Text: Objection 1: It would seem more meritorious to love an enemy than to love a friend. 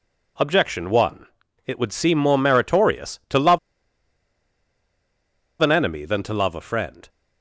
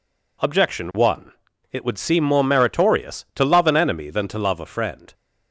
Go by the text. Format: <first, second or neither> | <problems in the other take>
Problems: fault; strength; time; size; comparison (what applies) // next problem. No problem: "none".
second | pauses between "love" and "an"; strong; at 3.5 s; 2.0 s long